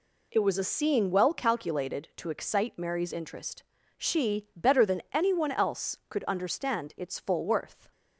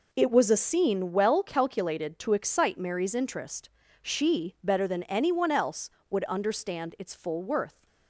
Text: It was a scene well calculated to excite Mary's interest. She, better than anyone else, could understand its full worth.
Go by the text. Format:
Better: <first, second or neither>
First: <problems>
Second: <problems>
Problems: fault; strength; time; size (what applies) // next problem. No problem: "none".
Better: first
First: none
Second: says "would" for "could"; at 6.0 s